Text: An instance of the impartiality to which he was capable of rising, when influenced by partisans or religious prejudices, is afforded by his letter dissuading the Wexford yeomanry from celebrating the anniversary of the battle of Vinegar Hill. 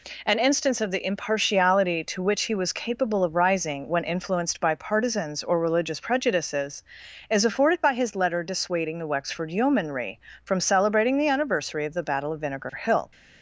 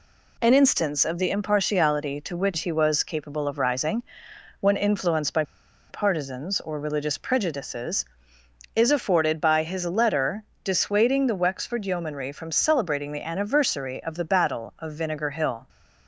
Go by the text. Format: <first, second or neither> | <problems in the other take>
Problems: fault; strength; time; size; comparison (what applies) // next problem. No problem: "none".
first | pauses between "by" and "partisans"; noticeable; at 5.4 s; 0.47 s long // pauses between "letter" and "dissuading"; slight; at 10.4 s; 0.22 s long